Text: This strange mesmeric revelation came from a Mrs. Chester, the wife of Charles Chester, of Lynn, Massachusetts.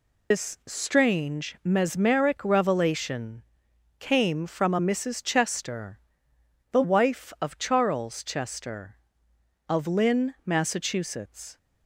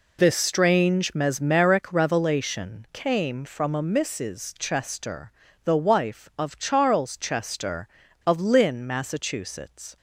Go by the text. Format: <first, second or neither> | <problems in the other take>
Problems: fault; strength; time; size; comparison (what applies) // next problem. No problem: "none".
second | loses the start of "This"; at 0.3 s; 125 ms // pauses between "revelation" and "came"; noticeable; at 3.4 s; 0.58 s long